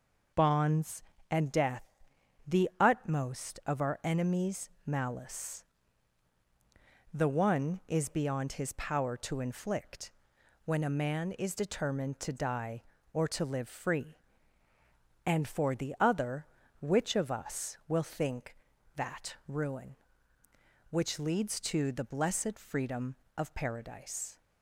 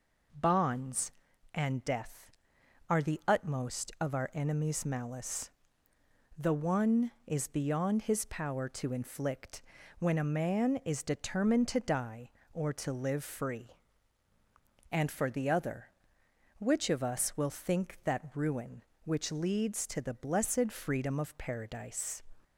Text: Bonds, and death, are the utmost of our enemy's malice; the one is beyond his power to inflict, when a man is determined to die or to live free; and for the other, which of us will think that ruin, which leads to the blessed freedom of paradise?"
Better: second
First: skips "are"; at 2.1 s // pauses between "enemy's" and "malice"; slight; at 4.6 s; 0.18 s long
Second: none

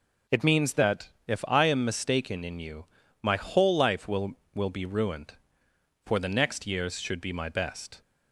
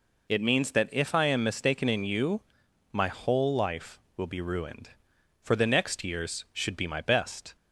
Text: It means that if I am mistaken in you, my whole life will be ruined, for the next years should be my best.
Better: second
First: pauses between "that" and "if"; slight; at 1.0 s; 0.16 s long // says "will" twice; at 4.5 s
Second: none

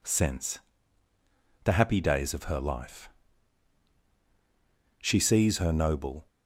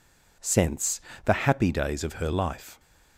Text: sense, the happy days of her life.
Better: second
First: goes on to say "She sees her noble"; noticeable; from 5.0 s on; 1.2 s long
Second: none

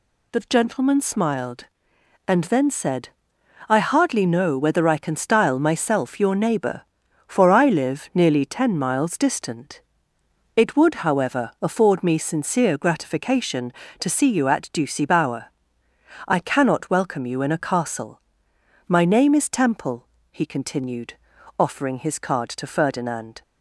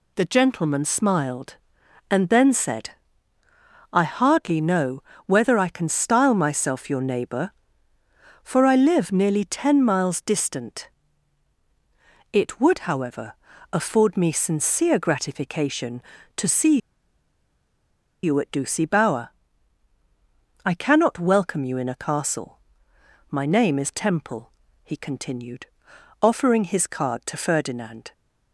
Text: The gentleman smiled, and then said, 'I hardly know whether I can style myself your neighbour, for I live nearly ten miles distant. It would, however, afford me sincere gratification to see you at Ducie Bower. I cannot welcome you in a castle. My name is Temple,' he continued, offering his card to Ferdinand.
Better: first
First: none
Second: pauses between "know" and "whether"; slight; at 5.0 s; 0.22 s long // pauses between "see" and "you"; strong; at 16.7 s; 1.4 s long

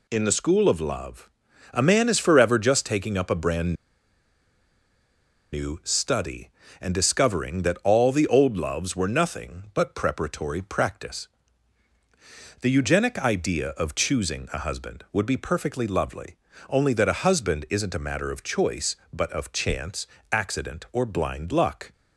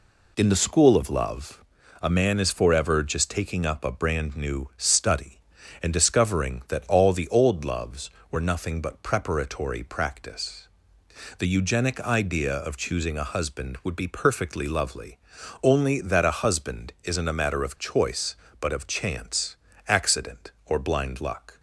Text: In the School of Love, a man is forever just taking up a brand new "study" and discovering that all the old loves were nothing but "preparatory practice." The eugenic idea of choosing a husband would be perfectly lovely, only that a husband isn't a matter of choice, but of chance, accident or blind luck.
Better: second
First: pauses between "brand" and "new"; strong; at 3.7 s; 1.7 s long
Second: none

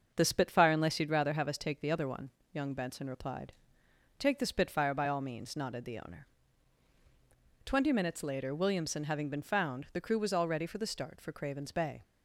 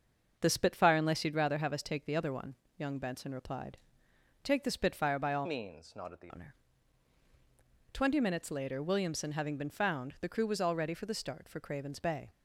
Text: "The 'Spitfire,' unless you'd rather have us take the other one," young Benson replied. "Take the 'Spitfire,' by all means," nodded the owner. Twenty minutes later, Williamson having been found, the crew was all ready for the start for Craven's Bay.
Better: first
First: starts louder than the rest; until 1.1 s; 6.5 dB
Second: starts louder than the rest; until 1.4 s; 6.5 dB // changes voice from "means" to "the"; from 5.4 to 6.3 s; 0.9 s long

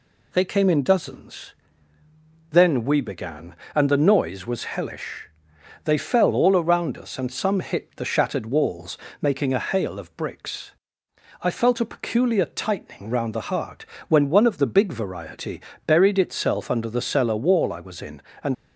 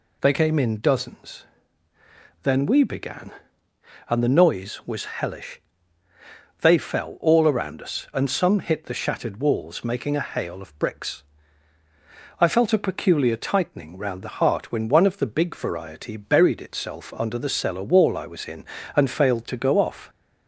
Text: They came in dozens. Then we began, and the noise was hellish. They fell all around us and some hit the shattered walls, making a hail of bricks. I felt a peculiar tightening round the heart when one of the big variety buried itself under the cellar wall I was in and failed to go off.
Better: second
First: pauses between "heart" and "when"; slight; at 13.8 s; 0.24 s long // pauses between "variety" and "buried"; slight; at 15.6 s; 0.26 s long // stops before "failed to go off"; at 18.5 s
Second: none

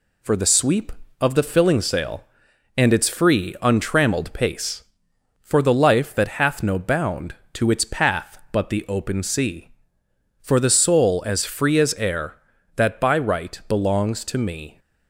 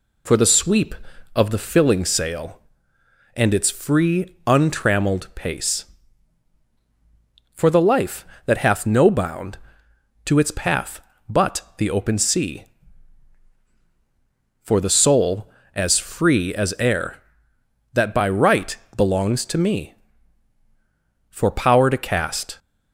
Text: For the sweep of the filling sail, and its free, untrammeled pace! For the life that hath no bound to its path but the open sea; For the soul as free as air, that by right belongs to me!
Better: first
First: none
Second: pauses between "right" and "belongs"; slight; at 18.7 s; 0.20 s long // goes on to say "For power to cast"; noticeable; from 21.3 s on; 1.2 s long

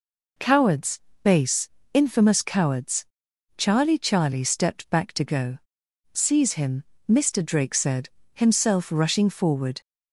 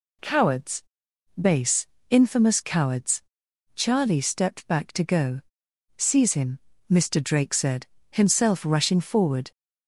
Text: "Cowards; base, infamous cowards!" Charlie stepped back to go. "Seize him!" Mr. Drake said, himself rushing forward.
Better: second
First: says "Charlie" twice; at 3.9 s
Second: none

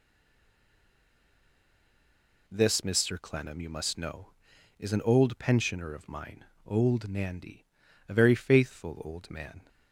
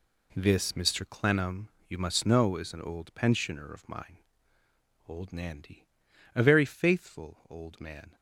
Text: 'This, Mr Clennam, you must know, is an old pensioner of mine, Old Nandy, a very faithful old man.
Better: second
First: stays silent before the first word; until 2.4 s; 2.4 s long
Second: none

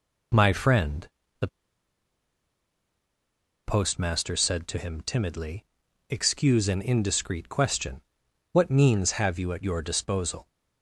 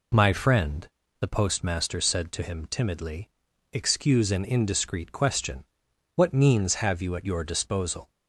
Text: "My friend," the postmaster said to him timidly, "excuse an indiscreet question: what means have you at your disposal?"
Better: second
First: pauses between "the" and "postmaster"; strong; at 1.4 s; 2.1 s long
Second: none

